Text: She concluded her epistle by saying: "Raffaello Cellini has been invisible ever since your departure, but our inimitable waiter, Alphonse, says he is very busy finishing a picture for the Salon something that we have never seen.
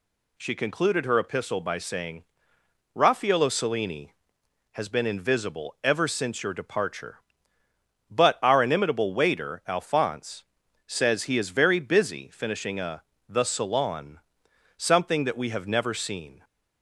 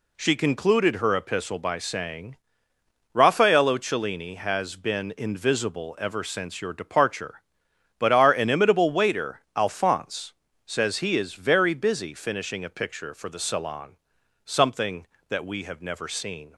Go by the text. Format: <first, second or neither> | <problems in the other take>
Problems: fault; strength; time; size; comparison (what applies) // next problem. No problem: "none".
second | skips "picture for"; at 13.1 s // pauses between "Salon" and "something"; noticeable; at 14.1 s; 0.60 s long; noticeable in the second